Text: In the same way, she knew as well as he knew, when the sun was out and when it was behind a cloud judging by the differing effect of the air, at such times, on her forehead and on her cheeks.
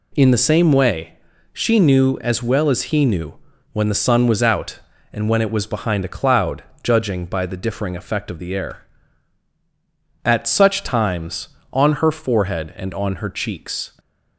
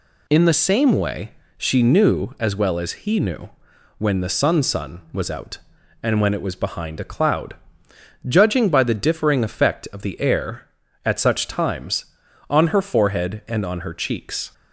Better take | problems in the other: first | says "sun" twice; at 4.6 s // pauses between "cloud" and "judging"; noticeable; at 7.5 s; 0.72 s long; slight in the first

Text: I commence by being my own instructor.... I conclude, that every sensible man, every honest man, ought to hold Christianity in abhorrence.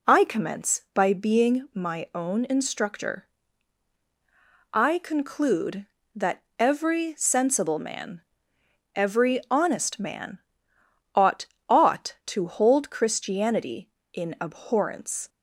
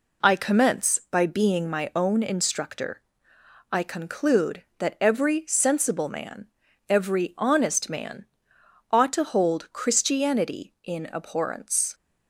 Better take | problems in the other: second | pauses between "that" and "every"; slight; at 6.4 s; 0.18 s long // says "ought" twice; at 11.6 s

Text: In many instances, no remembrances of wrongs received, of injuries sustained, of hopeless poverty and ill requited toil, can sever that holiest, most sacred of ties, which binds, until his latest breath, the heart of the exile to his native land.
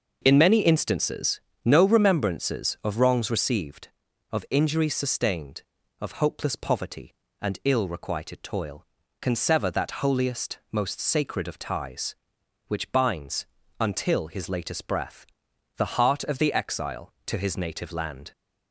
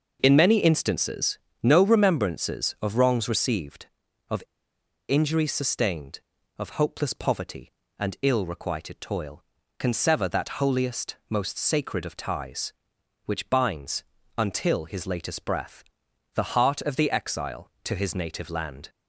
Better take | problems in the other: first | pauses between "of" and "injuries"; noticeable; at 4.4 s; 0.66 s long

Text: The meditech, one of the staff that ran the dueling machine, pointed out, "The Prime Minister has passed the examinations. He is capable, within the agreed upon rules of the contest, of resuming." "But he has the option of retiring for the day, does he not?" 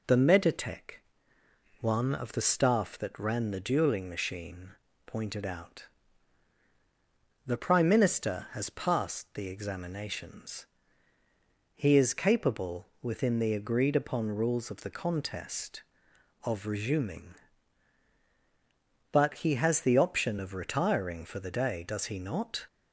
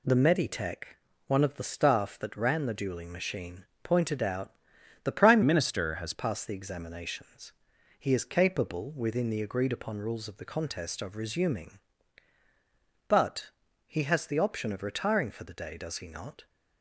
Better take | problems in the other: first | changes voice from "Minister" to "has"; from 5.4 to 6.1 s; 0.7 s long // pauses between "But" and "he"; slight; at 13.4 s; 0.36 s long

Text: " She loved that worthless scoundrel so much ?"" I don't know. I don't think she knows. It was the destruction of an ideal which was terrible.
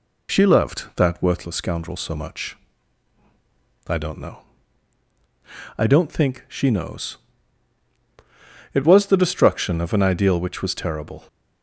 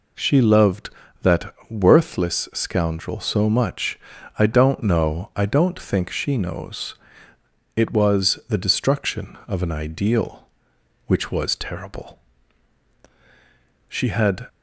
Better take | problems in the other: first | pauses between "that" and "worthless"; slight; at 1.5 s; 0.18 s long // goes on to say "She had"; from 13.8 s on; 0.58 s long

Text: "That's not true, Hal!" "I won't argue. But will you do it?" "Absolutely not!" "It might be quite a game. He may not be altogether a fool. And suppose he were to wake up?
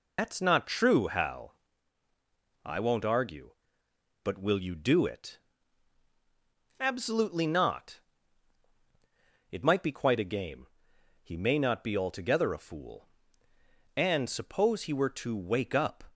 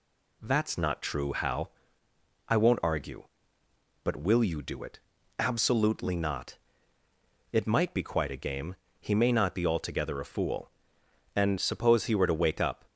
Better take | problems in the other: second | loses the start of "That's"; at 0.1 s; 150 ms

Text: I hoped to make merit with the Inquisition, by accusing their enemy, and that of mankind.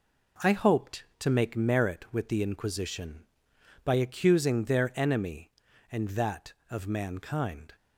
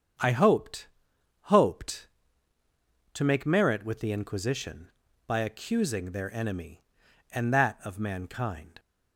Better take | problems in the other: first | starts louder than the rest; strong; until 1.7 s; 7.5 dB // says "hoped" twice; at 1.4 s

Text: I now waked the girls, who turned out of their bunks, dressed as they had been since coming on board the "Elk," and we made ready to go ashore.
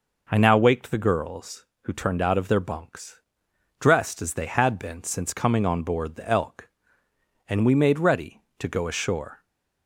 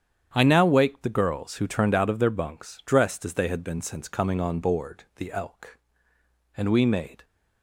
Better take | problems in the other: first | starts louder than the rest; strong; until 1.3 s; 8.5 dB // stops before "ready to go ashore"; at 7.2 s

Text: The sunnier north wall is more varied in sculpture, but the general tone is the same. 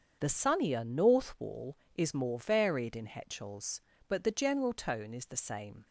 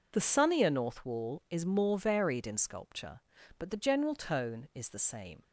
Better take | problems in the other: second | starts louder than the rest; strong; until 1.2 s; 7 dB // says "hetchels" for "sculpture"; at 3.0 s

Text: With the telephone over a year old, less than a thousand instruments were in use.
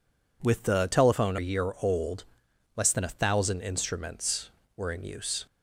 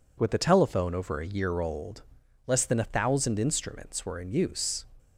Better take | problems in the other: second | skips "over"; at 1.3 s

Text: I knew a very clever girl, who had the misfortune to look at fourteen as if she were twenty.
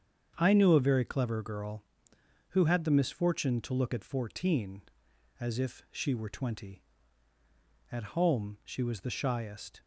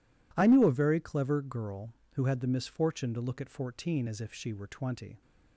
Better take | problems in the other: second | starts louder than the rest; strong; until 1.3 s; 7.5 dB // goes on to say "At home she was the shyest"; strong; from 7.9 s on; 1.9 s long

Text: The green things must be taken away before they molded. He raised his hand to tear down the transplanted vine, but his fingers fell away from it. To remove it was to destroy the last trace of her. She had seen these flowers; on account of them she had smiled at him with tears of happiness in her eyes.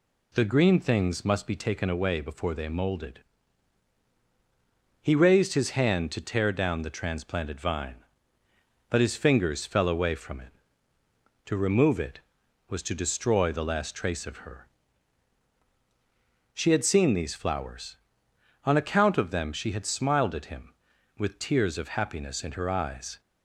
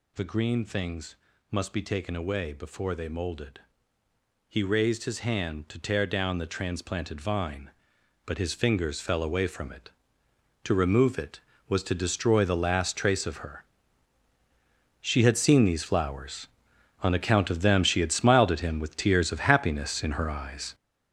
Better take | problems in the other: first | gets louder; strong; throughout; 8.5 dB // pauses between "things" and "must"; slight; at 1.1 s; 0.36 s long

